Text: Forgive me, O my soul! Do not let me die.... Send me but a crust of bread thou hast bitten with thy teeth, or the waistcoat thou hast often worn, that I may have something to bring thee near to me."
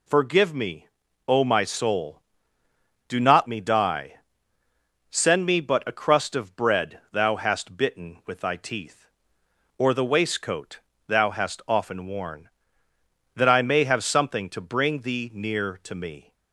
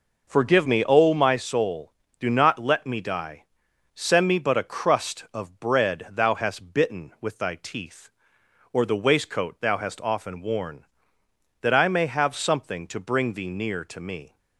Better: second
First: skips "let"; at 3.4 s // pauses between "waistcoat" and "thou"; slight; at 10.7 s; 0.28 s long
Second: none

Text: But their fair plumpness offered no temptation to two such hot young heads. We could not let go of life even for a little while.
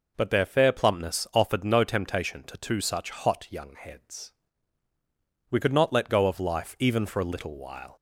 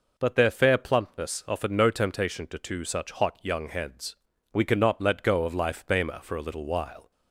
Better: first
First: none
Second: says "bema" for "even"; at 5.8 s

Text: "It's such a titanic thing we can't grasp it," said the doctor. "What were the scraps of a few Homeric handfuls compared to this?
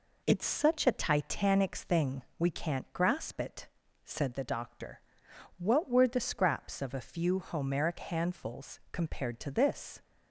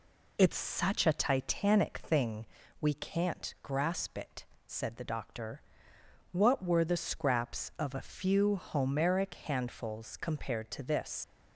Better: first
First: pauses between "thing" and "we"; slight; at 2.2 s; 0.18 s long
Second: pauses between "thing" and "we"; slight; at 2.4 s; 0.34 s long // leaves "this" unfinished; at 11.2 s; 115 ms

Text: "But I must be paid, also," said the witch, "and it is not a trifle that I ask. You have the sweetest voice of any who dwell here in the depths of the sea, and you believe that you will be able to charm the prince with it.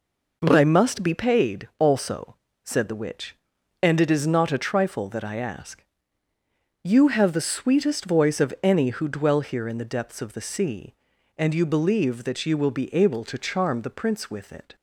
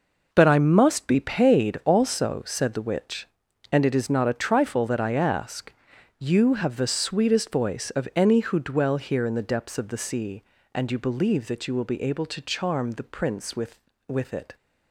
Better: first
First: none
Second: says "with" twice; at 14.0 s

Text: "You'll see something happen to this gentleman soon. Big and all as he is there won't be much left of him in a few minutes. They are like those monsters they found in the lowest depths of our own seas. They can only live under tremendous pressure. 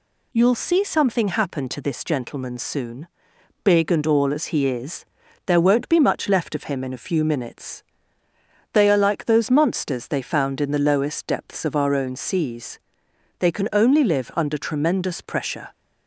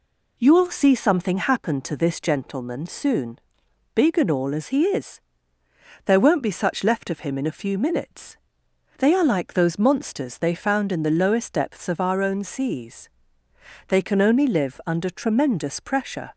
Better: first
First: pauses between "is" and "there"; at 5.0 s; 0.42 s long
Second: pauses between "is" and "there"; noticeable; at 5.1 s; 0.84 s long // says "such" for "much"; at 6.5 s

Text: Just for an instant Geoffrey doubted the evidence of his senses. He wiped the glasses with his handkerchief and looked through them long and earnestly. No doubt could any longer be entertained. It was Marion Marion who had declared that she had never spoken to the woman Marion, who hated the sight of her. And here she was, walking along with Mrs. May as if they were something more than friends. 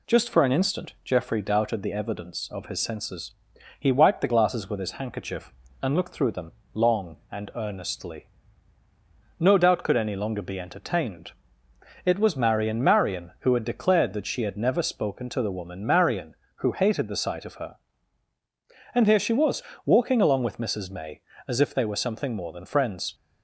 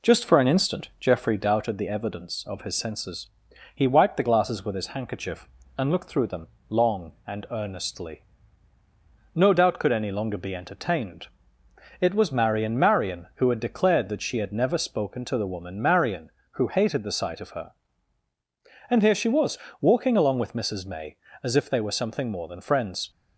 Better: first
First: pauses between "them" and "long"; slight; at 6.5 s; 0.20 s long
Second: starts louder than the rest; slight; until 1.6 s; 3 dB // pauses between "them" and "long"; slight; at 6.4 s; 0.20 s long

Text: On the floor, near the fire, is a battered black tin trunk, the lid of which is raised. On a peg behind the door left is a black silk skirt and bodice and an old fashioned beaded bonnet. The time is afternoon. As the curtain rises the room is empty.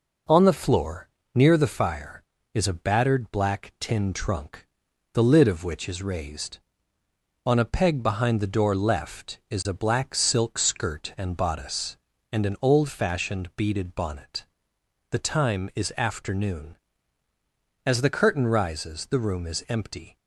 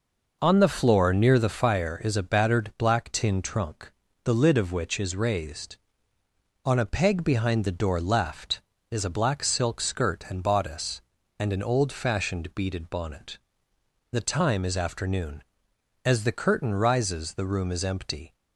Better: neither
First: none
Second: none

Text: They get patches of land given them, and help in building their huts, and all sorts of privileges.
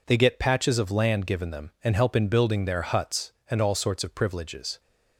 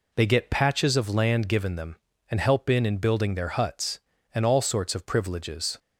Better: first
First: none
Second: says "in" twice; at 2.8 s

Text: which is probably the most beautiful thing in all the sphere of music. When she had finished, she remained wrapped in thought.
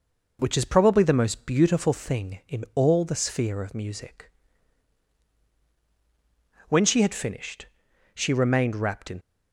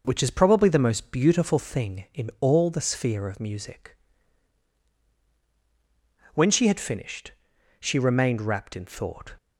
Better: second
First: stops before "thought"; at 9.2 s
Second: none

